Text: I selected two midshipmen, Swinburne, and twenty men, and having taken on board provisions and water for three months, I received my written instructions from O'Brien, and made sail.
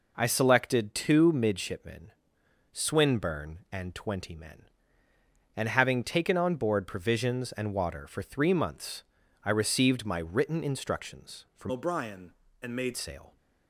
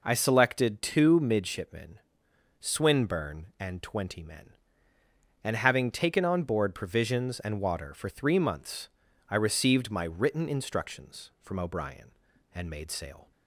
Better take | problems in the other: second | changes voice from "O'Brien" to "made"; from 11.7 to 12.9 s; 1.2 s long

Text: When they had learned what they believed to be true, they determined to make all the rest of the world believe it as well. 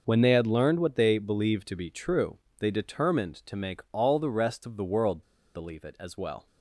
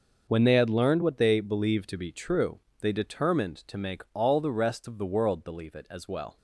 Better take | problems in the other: second | pauses between "world" and "believe"; slight; at 5.2 s; 0.30 s long

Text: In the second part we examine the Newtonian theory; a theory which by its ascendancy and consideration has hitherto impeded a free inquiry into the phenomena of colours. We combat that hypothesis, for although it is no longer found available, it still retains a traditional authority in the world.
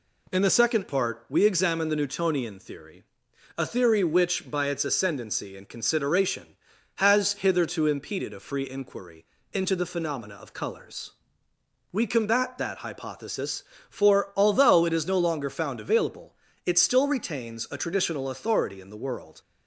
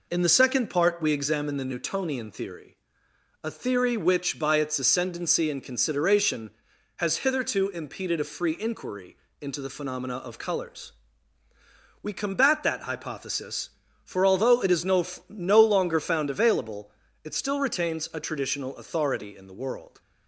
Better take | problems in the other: first | pauses between "inquiry" and "into"; slight; at 9.1 s; 0.22 s long; slight in the first // says "no" twice; at 15.2 s

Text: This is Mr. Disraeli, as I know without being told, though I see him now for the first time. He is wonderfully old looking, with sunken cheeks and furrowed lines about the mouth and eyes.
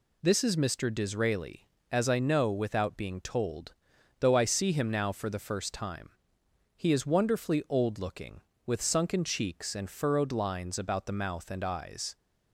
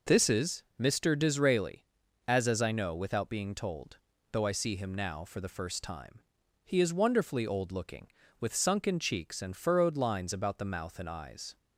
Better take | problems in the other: first | says "as" twice; at 2.4 s

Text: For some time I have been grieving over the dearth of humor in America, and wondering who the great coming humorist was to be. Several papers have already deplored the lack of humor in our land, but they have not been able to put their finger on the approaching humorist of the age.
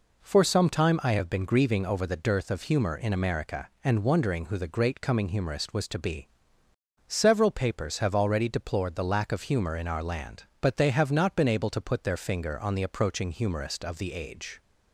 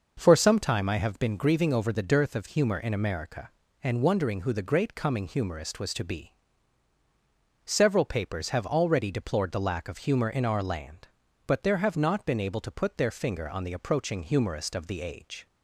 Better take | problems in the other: first | says "there" for "they"; at 11.6 s

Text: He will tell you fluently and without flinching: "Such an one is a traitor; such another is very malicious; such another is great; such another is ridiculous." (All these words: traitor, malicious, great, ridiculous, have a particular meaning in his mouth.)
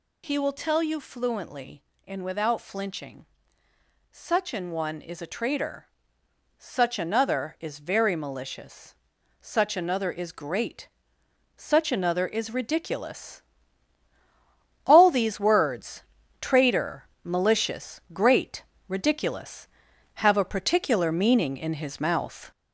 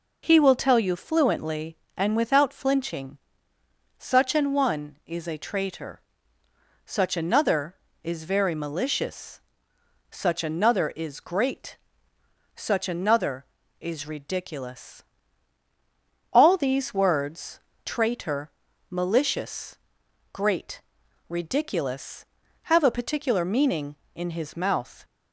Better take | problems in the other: second | gets louder; noticeable; throughout; 5 dB

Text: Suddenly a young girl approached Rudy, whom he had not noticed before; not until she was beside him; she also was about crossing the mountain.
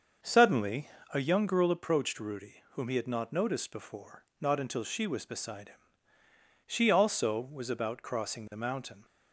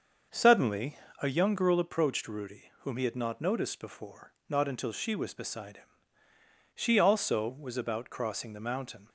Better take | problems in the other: neither | starts louder than the rest; the same in both // pauses between "Suddenly" and "a"; slight; the same in both

